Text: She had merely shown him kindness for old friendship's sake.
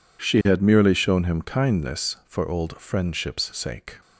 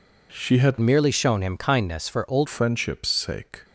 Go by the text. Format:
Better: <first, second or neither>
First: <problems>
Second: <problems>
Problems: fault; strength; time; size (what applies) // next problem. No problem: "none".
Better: first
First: none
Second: changes voice from "merely" to "old"; from 0.8 to 2.4 s; 1.6 s long